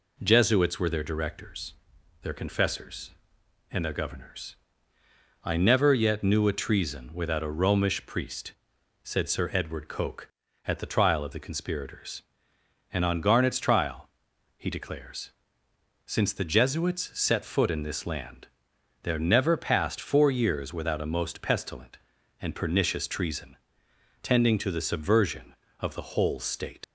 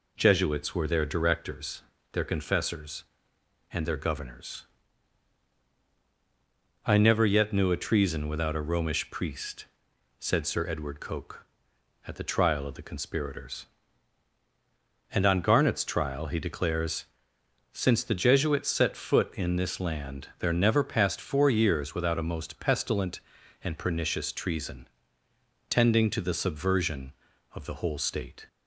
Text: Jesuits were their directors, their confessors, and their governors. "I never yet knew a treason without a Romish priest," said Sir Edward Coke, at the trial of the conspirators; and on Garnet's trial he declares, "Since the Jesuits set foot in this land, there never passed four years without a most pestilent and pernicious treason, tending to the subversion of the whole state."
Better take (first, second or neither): second